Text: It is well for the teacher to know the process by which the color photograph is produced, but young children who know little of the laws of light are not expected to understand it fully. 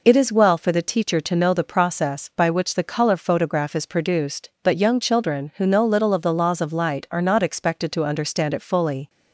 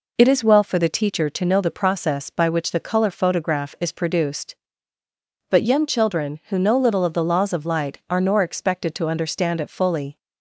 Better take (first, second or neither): first